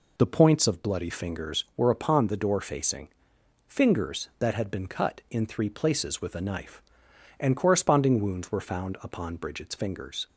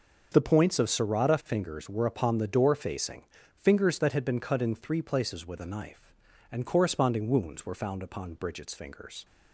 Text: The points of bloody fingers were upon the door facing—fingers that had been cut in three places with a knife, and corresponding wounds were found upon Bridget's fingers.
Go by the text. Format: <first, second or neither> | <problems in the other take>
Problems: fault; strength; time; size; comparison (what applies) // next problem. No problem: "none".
first | starts louder than the rest; until 1.3 s; 6.5 dB // says "serrata" for "bloody"; at 0.8 s